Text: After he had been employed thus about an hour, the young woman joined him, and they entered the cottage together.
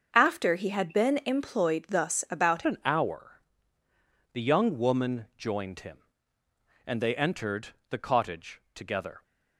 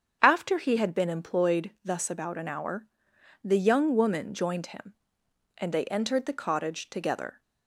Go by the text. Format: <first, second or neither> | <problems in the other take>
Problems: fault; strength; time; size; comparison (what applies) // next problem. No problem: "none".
second | starts louder than the rest; until 1.1 s; 6.5 dB; strong in the second // changes voice at "an"; from 2.6 s on; 6.6 s long // pauses between "entered" and "the"; slight; at 7.6 s; 0.20 s long